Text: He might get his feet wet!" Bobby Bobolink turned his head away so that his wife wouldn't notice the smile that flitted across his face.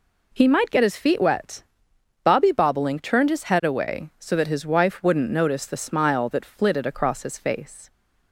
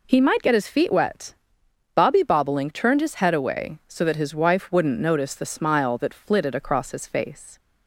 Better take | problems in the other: neither | none

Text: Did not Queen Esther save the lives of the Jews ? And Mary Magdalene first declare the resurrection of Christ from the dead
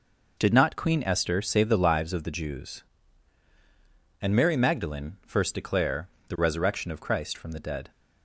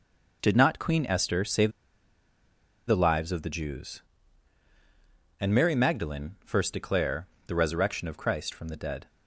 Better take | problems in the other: first | pauses between "save" and "the"; at 1.7 s; 1.1 s long // pauses between "declare" and "the"; slight; at 7.2 s; 0.20 s long; slight in the first

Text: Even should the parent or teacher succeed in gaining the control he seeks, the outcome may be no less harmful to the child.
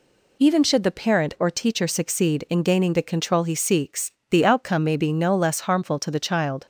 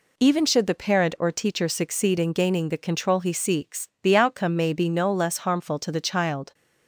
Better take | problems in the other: neither | none

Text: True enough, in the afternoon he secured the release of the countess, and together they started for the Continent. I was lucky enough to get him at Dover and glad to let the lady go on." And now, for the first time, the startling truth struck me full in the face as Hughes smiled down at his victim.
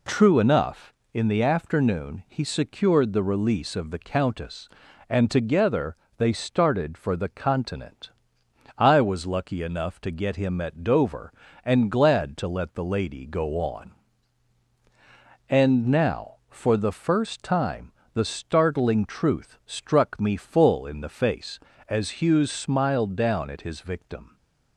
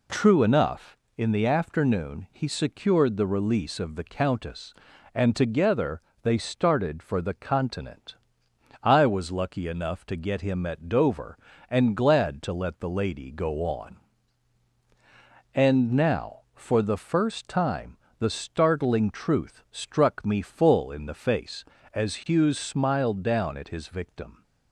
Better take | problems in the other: neither | pauses between "together" and "they"; slight; the same in both

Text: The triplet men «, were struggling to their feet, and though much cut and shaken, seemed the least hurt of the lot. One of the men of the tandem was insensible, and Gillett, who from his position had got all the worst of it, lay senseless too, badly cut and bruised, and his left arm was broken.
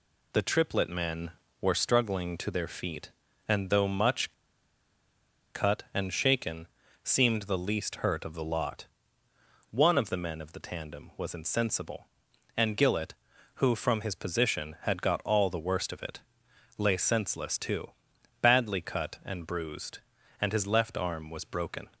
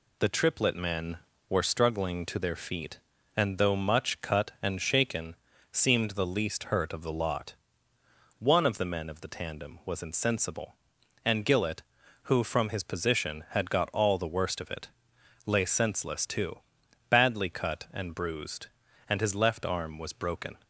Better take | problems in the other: second | pauses between "much" and "cut"; at 4.3 s; 1.2 s long

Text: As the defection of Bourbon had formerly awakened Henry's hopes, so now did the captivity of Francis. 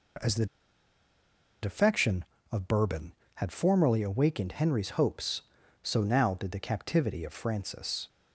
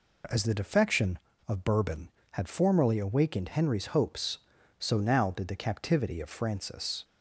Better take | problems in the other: second | pauses between "the" and "defection"; at 0.4 s; 1.1 s long

